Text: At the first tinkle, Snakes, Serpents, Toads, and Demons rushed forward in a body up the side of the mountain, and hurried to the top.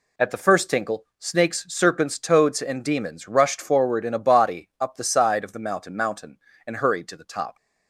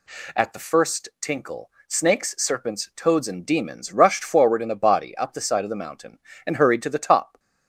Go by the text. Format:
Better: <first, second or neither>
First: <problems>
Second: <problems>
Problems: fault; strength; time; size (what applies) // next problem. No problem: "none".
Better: second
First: says "mountain" twice; at 5.9 s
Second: none